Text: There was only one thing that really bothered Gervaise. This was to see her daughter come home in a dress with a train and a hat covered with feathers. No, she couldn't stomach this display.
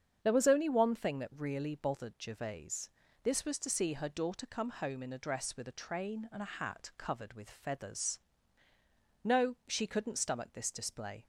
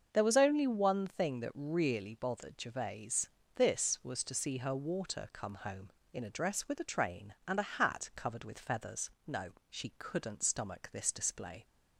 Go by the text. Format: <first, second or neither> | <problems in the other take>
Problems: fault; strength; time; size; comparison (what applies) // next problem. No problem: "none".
first | starts louder than the rest; until 1.1 s; 6.5 dB; strong in the first // says "water" for "daughter"; at 4.7 s